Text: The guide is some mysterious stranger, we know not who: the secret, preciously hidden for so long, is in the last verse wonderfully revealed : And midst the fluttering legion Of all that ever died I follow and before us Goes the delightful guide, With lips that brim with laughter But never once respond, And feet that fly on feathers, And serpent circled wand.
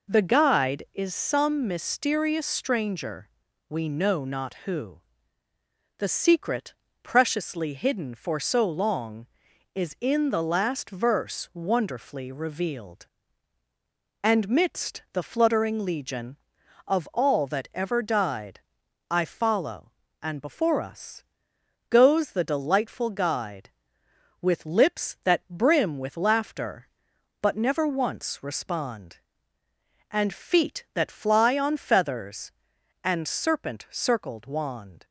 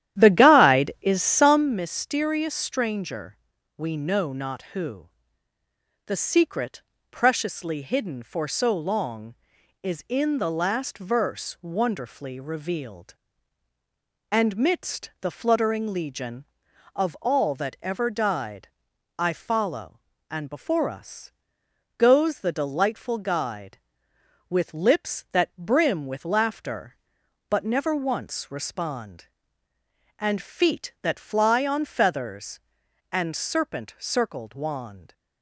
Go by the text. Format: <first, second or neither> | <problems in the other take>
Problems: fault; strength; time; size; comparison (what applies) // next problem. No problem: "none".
first | starts louder than the rest; strong; until 1.8 s; 11.5 dB // pauses between "died" and "I"; noticeable; at 18.6 s; 0.50 s long; noticeable in the first // pauses between "us" and "Goes"; noticeable; at 21.3 s; 0.68 s long; noticeable in the first